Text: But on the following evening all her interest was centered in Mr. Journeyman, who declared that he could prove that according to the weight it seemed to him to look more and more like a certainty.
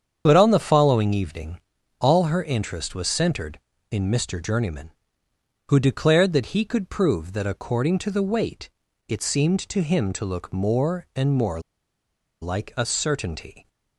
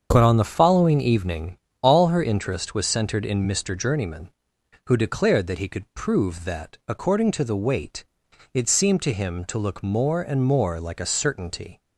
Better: second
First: starts louder than the rest; strong; until 1.2 s; 8 dB // pauses between "evening" and "all"; at 1.6 s; 0.40 s long // pauses between "weight" and "it"; at 8.6 s; 0.38 s long // pauses between "more" and "like"; noticeable; at 11.6 s; 0.81 s long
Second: starts louder than the rest; strong; until 1.1 s; 7 dB // pauses between "evening" and "all"; slight; at 1.5 s; 0.26 s long // pauses between "weight" and "it"; noticeable; at 8.0 s; 0.46 s long

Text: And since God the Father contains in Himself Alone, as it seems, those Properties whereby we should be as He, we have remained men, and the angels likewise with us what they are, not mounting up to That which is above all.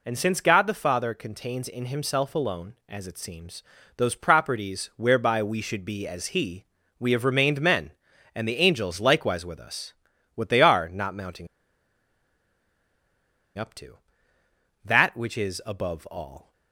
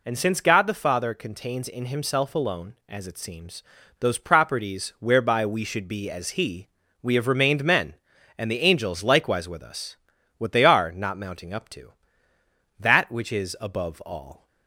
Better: second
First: pauses between "us" and "what"; at 9.9 s; 0.40 s long // pauses between "mounting" and "up"; strong; at 11.4 s; 2.1 s long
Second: pauses between "us" and "what"; at 9.9 s; 0.40 s long

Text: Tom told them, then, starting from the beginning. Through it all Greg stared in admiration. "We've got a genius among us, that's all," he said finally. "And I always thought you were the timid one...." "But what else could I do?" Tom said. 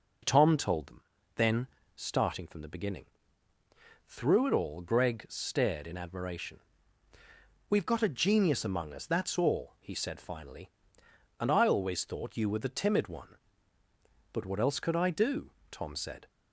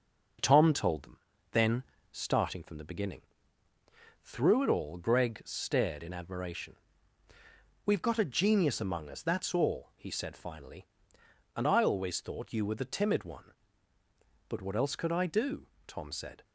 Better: first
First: none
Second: gets quieter; throughout; 4 dB

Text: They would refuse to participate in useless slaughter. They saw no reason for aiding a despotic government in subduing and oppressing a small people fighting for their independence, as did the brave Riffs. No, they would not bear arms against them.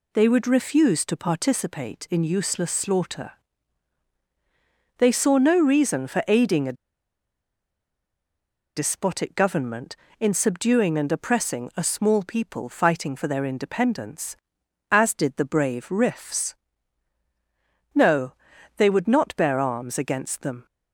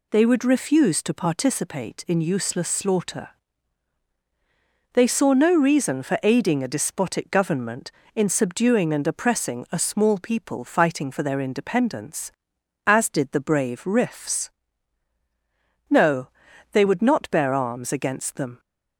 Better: second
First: pauses between "a" and "despotic"; strong; at 6.7 s; 2.0 s long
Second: none

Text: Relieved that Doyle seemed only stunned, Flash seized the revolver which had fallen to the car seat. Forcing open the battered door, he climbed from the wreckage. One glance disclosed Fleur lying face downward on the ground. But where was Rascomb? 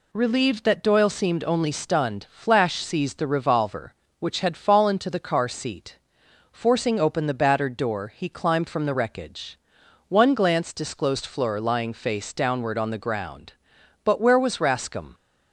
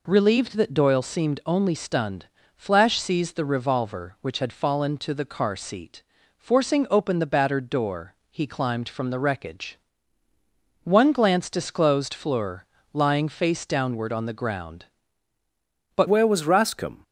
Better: first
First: none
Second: pauses between "Fleur" and "lying"; slight; at 12.6 s; 0.28 s long // changes voice at "where"; from 16.0 s on; 1.0 s long

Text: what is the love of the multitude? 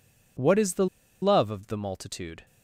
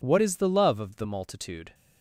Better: second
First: pauses between "the" and "love"; at 0.8 s; 0.36 s long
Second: none

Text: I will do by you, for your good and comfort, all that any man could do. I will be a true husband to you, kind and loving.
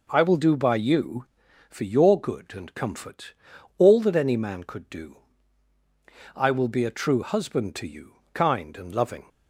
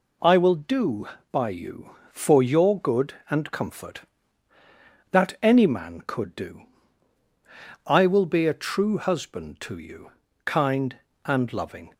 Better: first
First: none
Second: skips "all"; at 4.5 s

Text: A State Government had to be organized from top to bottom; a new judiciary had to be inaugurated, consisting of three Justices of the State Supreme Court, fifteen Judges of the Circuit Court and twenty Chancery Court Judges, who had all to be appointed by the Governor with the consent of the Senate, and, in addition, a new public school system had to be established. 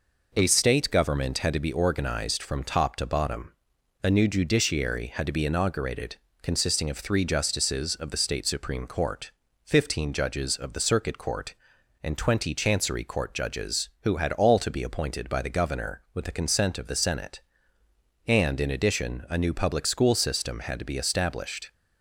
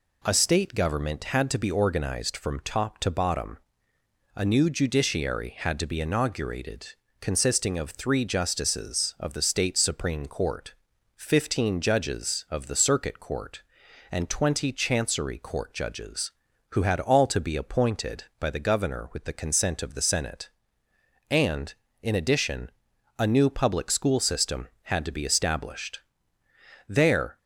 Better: first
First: none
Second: goes on to say "There"; from 26.8 s on; 0.50 s long

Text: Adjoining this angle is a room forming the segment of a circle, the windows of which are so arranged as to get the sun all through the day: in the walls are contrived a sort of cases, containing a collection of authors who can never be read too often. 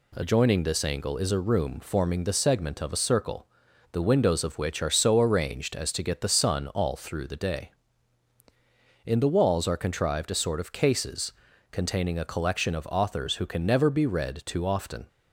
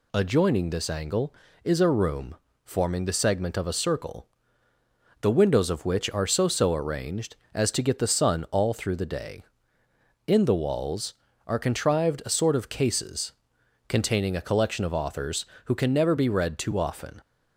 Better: first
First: none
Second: pauses between "room" and "forming"; slight; at 2.3 s; 0.30 s long // says "so" twice; at 6.4 s

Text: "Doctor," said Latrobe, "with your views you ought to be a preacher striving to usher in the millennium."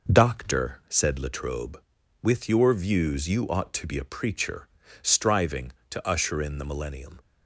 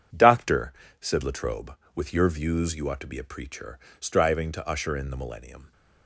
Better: neither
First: pauses between "preacher" and "striving"; slight; at 4.6 s; 0.32 s long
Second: pauses between "preacher" and "striving"; slight; at 3.7 s; 0.22 s long

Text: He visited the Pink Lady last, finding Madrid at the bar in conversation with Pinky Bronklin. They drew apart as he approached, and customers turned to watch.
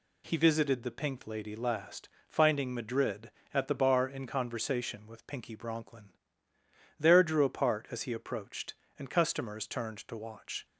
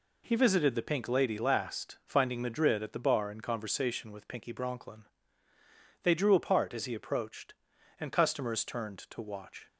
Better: second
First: says "There" for "They"; at 6.9 s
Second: none

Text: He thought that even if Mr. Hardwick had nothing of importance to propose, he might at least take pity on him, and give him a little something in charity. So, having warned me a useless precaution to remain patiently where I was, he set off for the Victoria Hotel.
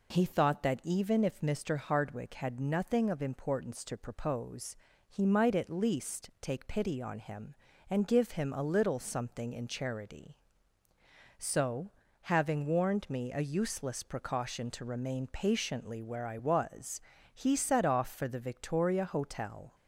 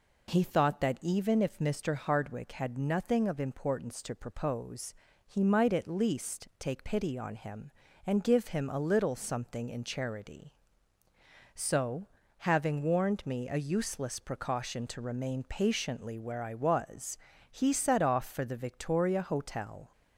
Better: neither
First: none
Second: none

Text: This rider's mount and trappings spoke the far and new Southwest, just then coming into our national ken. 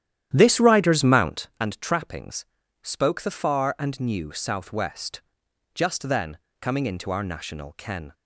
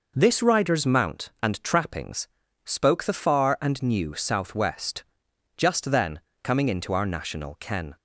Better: second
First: starts louder than the rest; strong; until 1.6 s; 11 dB // pauses between "trappings" and "spoke"; slight; at 2.4 s; 0.36 s long // pauses between "then" and "coming"; slight; at 6.3 s; 0.24 s long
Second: pauses between "trappings" and "spoke"; slight; at 2.2 s; 0.36 s long // pauses between "then" and "coming"; slight; at 6.2 s; 0.24 s long

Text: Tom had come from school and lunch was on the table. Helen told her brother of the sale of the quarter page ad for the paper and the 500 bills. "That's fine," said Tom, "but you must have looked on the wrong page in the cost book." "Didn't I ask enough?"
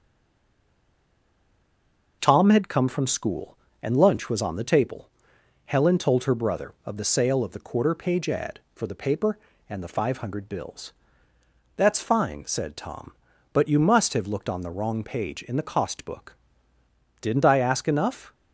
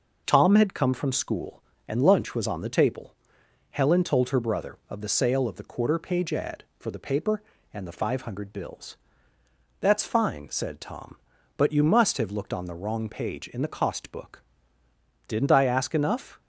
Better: second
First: stays silent before the first word; until 2.2 s; 2.2 s long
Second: none

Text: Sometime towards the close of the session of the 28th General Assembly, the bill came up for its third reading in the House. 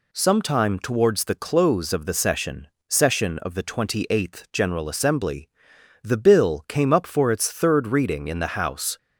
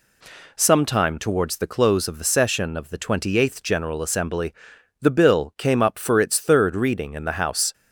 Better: second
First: says "session" twice; at 2.8 s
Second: none

